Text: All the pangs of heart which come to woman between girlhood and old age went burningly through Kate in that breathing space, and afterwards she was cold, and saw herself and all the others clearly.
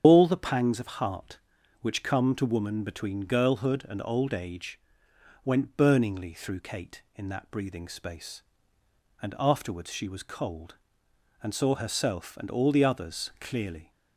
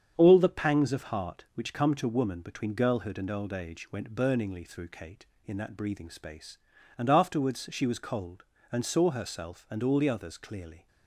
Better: second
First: loses the start of "All"; at 0.0 s; 110 ms // starts louder than the rest; strong; until 1.0 s; 8.5 dB // pauses between "age" and "went"; noticeable; at 4.8 s; 0.64 s long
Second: starts louder than the rest; strong; until 1.1 s; 7.5 dB

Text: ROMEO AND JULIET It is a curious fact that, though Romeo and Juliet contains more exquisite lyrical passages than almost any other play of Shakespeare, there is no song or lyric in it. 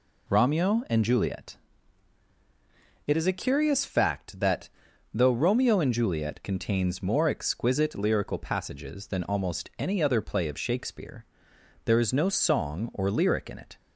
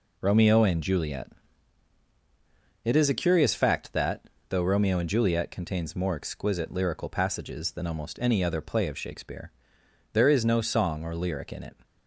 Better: neither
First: pauses between "JULIET" and "It"; strong; at 1.5 s; 1.5 s long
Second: pauses between "JULIET" and "It"; strong; at 1.3 s; 1.5 s long

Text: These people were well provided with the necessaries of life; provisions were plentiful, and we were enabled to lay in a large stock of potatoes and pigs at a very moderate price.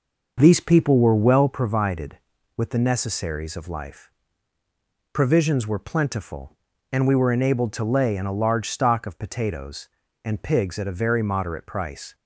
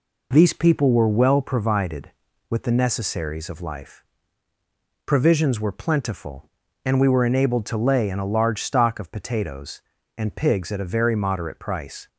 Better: second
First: starts louder than the rest; noticeable; until 1.5 s; 6 dB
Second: none

